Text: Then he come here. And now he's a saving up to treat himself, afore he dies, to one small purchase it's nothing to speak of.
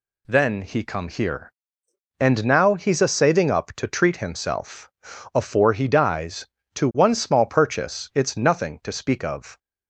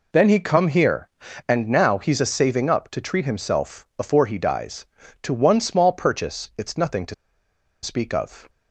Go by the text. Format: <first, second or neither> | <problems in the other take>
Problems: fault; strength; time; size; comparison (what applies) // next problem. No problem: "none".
first | pauses between "to" and "speak"; noticeable; at 7.1 s; 0.68 s long